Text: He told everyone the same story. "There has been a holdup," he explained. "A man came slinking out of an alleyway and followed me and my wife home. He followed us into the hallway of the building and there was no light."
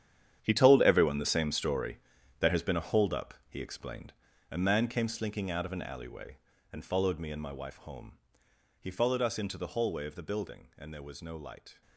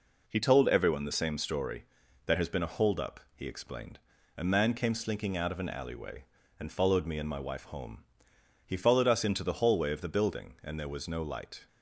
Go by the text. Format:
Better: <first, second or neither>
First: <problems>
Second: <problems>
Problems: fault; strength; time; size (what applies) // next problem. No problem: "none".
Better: second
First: gets quieter; strong; throughout; 13.5 dB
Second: none